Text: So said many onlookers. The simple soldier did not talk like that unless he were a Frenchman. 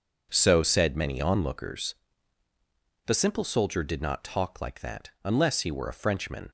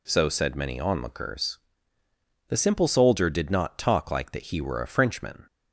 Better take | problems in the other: first | skips "unless"; at 4.5 s

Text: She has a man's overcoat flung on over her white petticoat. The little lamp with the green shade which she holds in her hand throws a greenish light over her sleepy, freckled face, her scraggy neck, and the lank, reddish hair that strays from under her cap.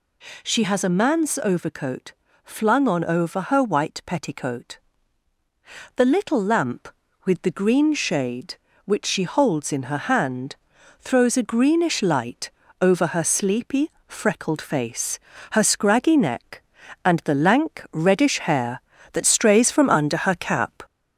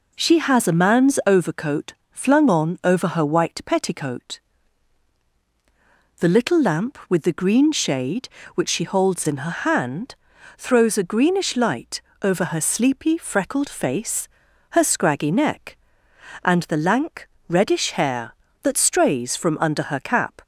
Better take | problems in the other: second | gets louder; slight; throughout; 2 dB // pauses between "overcoat" and "flung"; slight; at 2.1 s; 0.32 s long; slight in the second // pauses between "hand" and "throws"; at 10.5 s; 0.44 s long; also in the second // pauses between "light" and "over"; slight; at 12.4 s; 0.32 s long; slight in the second

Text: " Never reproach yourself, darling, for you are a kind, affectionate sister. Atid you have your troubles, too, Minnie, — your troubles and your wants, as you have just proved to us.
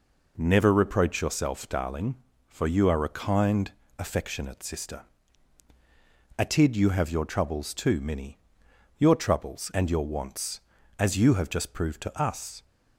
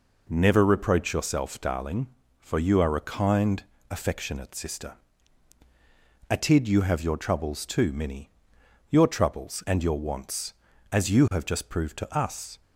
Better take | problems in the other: neither | none

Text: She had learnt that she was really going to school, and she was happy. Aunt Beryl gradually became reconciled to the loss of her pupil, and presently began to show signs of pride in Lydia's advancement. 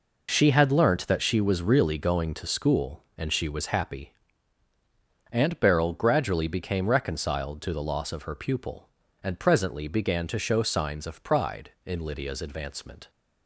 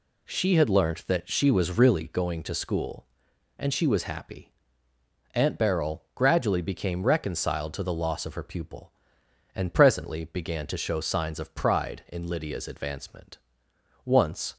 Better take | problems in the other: first | goes on to say "Once"; from 14.0 s on; 0.52 s long

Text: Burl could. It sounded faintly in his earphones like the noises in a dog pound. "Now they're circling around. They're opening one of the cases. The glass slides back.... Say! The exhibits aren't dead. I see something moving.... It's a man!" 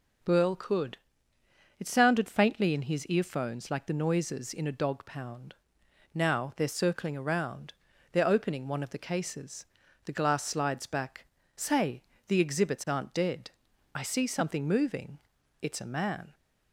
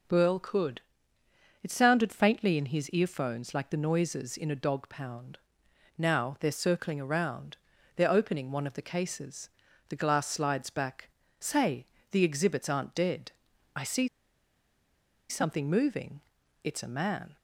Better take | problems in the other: first | pauses between "see" and "something"; at 14.0 s; 1.2 s long

